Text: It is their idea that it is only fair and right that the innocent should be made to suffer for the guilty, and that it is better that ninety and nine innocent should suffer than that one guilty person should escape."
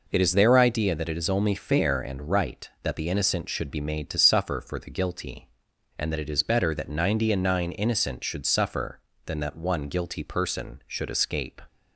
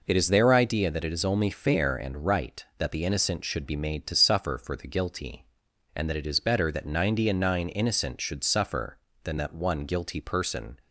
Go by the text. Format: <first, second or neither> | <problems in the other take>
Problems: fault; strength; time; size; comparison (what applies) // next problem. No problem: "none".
first | stops before "should escape"; at 10.8 s